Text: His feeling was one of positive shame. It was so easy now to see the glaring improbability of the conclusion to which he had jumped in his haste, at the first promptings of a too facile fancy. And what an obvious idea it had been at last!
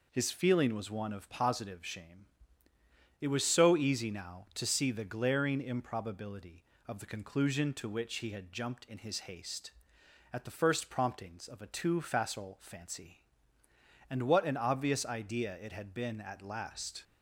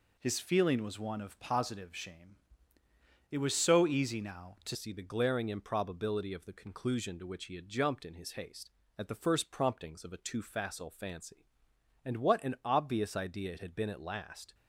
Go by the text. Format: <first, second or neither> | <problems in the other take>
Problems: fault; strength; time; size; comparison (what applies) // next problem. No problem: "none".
first | changes voice at "see"; from 4.7 s on; 9.8 s long